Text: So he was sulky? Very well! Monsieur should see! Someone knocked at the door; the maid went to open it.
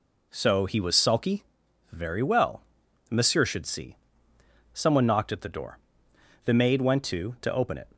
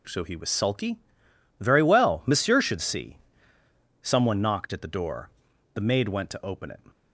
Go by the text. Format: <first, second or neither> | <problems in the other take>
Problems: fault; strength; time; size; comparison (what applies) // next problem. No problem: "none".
second | says "to" twice; at 7.4 s